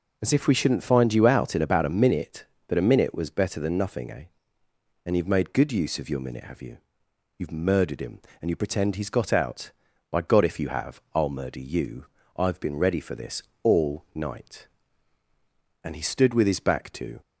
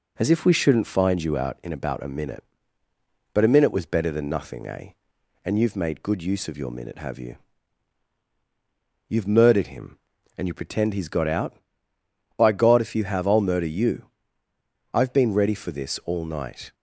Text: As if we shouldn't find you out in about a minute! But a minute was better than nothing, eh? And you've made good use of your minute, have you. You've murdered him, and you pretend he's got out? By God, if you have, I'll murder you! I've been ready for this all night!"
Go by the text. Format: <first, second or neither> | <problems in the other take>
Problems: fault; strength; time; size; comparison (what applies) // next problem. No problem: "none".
second | pauses between "this" and "all"; slight; at 13.4 s; 0.20 s long // goes on to say "And he stood with his back to"; from 15.8 s on; 1.3 s long